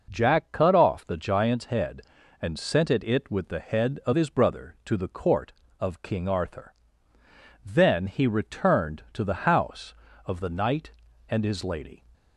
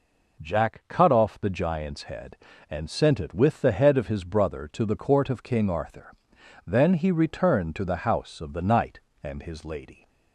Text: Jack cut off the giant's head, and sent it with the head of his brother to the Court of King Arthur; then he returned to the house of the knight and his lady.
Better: second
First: says "it" twice; at 3.0 s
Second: none

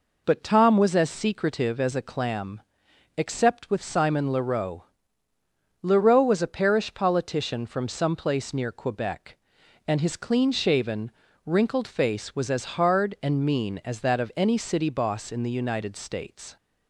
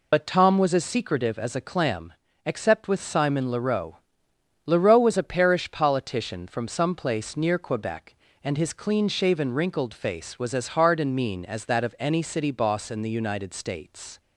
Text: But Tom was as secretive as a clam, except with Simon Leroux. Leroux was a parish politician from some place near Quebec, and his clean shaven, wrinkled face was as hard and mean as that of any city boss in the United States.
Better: first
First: none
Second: loses the start of "But"; at 0.1 s; 65 ms

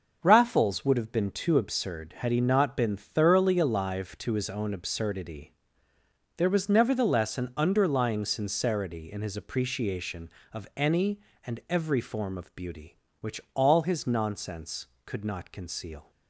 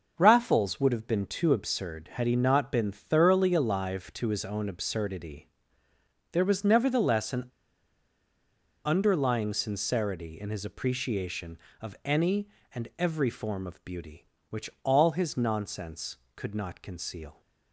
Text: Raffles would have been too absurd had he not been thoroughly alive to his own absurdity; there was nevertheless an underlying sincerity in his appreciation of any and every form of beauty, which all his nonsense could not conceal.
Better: first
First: starts louder than the rest; noticeable; until 1.2 s; 6 dB // pauses between "which" and "all"; slight; at 13.3 s; 0.16 s long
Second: starts louder than the rest; noticeable; until 1.1 s; 6 dB // pauses between "an" and "underlying"; strong; at 7.4 s; 1.3 s long // pauses between "which" and "all"; slight; at 14.6 s; 0.16 s long

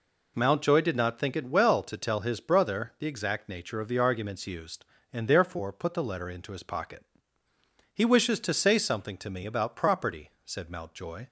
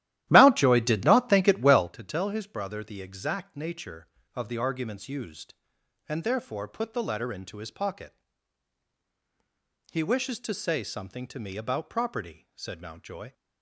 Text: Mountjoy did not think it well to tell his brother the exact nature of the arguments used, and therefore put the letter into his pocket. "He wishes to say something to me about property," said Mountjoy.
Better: first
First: none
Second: starts louder than the rest; strong; until 1.9 s; 13.5 dB

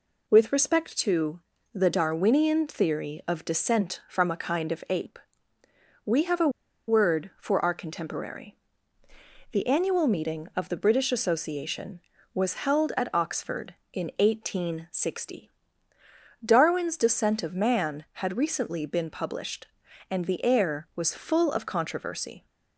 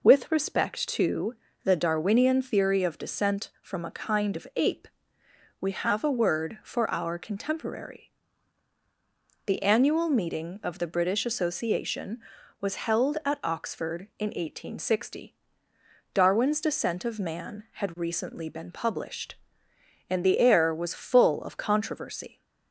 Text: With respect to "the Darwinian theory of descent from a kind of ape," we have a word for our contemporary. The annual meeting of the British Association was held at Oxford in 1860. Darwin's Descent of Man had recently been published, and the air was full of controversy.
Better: second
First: pauses between "to" and "the"; slight; at 1.3 s; 0.34 s long // pauses between "a" and "word"; at 6.4 s; 0.39 s long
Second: pauses between "to" and "the"; slight; at 1.3 s; 0.28 s long

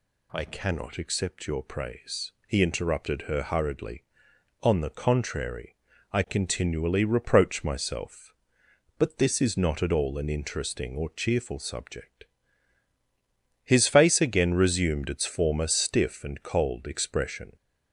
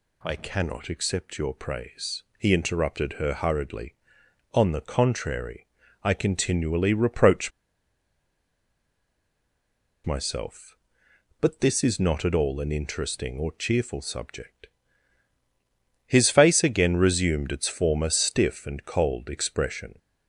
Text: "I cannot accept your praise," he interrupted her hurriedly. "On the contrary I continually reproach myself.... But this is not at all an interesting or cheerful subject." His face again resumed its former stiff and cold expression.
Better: first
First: pauses between "contrary" and "I"; slight; at 5.7 s; 0.36 s long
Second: pauses between "contrary" and "I"; slight; at 5.6 s; 0.36 s long // pauses between "reproach" and "myself"; strong; at 7.5 s; 2.5 s long

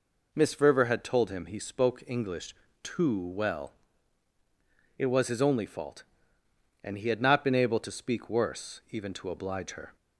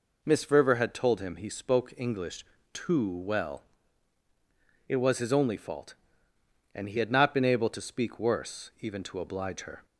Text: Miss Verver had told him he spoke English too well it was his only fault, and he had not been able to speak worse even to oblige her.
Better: neither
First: pauses between "English" and "too"; slight; at 2.5 s; 0.28 s long // pauses between "well" and "it"; at 3.7 s; 1.2 s long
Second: pauses between "English" and "too"; slight; at 2.4 s; 0.28 s long // pauses between "well" and "it"; at 3.6 s; 1.2 s long

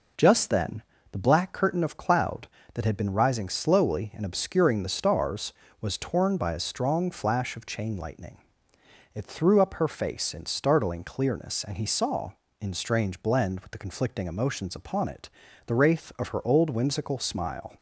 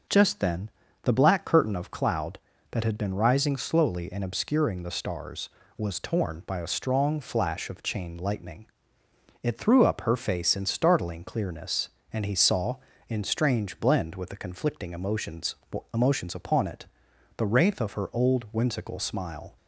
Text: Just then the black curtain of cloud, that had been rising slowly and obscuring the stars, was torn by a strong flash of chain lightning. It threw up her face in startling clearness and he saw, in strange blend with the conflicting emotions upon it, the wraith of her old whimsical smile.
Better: first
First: pauses between "then" and "the"; slight; at 0.8 s; 0.28 s long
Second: pauses between "then" and "the"; slight; at 0.6 s; 0.34 s long // says "emotions" twice; at 15.9 s

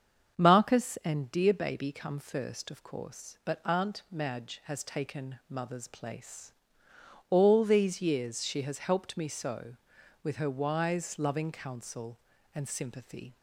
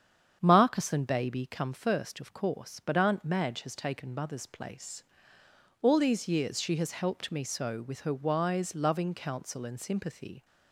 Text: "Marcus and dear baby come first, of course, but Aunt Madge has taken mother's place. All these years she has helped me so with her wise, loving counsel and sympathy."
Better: first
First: starts louder than the rest; strong; until 1.4 s; 7 dB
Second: starts louder than the rest; strong; until 1.4 s; 8 dB // skips "dear"; at 1.0 s

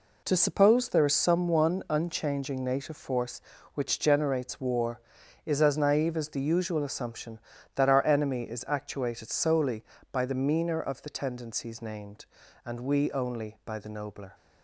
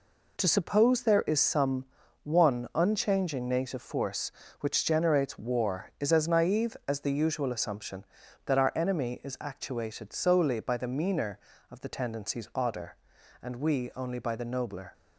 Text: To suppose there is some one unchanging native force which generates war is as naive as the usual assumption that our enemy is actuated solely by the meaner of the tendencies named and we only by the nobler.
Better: first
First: none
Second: pauses between "some" and "one"; at 1.8 s; 0.38 s long // says "odder" for "named"; at 12.5 s

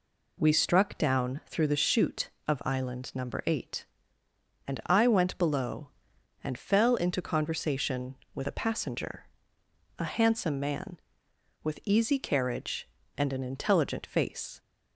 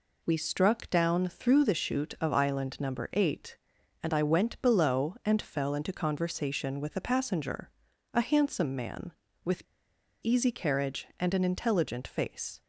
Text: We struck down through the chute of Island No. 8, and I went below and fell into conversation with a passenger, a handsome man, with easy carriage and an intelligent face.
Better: first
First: none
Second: pauses between "with" and "easy"; noticeable; at 9.6 s; 0.58 s long

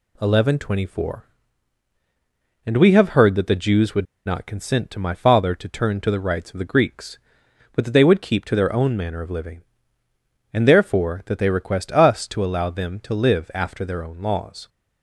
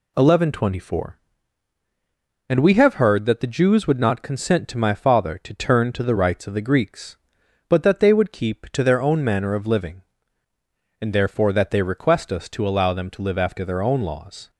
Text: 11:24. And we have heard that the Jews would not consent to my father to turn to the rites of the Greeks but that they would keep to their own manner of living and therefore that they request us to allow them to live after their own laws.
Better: second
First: pauses between "would" and "not"; slight; at 4.0 s; 0.20 s long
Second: none

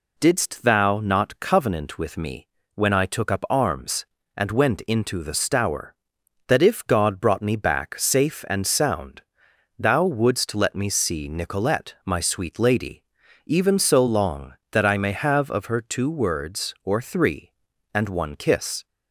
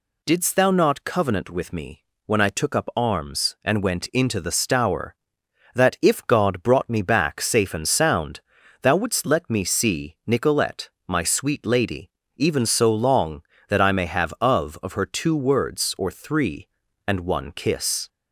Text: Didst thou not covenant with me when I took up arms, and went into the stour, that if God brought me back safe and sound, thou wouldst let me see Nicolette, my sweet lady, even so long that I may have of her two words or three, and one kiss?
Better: first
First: pauses between "me" and "when"; slight; at 2.4 s; 0.28 s long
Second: pauses between "me" and "when"; slight; at 2.0 s; 0.22 s long // says "of" twice; at 14.8 s

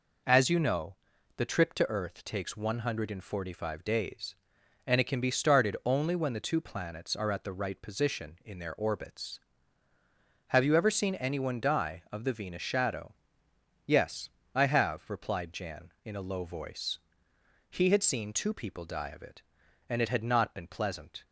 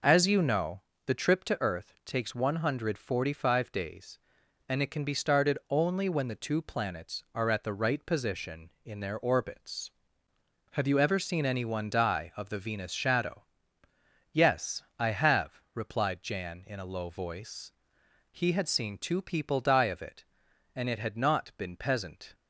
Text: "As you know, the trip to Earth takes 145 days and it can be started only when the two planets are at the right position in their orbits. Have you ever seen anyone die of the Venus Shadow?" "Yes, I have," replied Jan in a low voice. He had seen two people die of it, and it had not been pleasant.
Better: first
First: none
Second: says "peasant" for "pleasant"; at 21.7 s

